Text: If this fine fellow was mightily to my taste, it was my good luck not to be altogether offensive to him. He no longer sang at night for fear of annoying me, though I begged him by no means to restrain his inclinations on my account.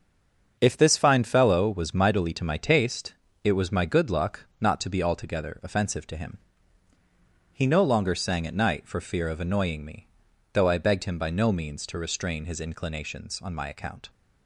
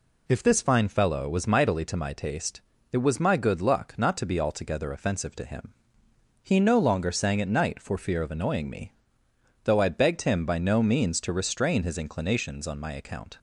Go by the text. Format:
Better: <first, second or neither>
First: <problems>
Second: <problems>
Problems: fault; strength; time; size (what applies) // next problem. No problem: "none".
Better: second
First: stays silent before the first word; slight; until 0.5 s; 0.5 s long // starts louder than the rest; strong; until 1.6 s; 7 dB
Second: none